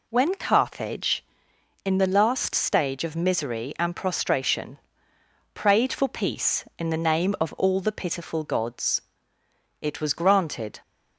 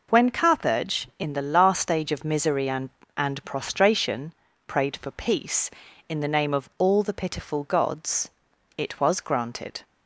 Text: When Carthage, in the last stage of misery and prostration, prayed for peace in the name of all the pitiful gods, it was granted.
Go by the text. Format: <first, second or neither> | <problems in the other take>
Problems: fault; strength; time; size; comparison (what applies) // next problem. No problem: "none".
first | says "and" twice; at 3.1 s